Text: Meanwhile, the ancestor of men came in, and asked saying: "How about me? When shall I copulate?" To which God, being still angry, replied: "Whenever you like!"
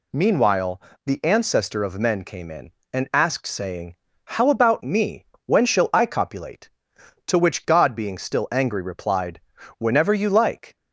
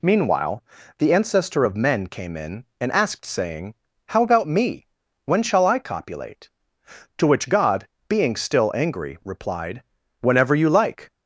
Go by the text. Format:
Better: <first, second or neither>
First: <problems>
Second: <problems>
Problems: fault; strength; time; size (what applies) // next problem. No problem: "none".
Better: neither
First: none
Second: none